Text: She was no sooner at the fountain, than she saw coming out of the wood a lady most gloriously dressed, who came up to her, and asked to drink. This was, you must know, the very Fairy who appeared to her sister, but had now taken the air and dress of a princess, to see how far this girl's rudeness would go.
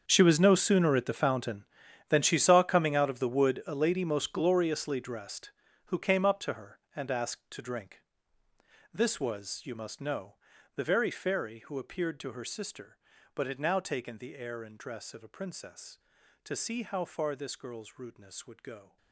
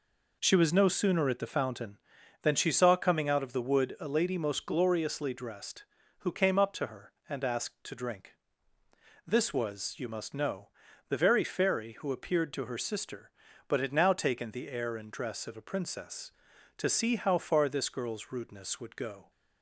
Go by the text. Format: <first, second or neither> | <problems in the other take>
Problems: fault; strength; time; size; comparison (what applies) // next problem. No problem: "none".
second | gets quieter; strong; throughout; 17.5 dB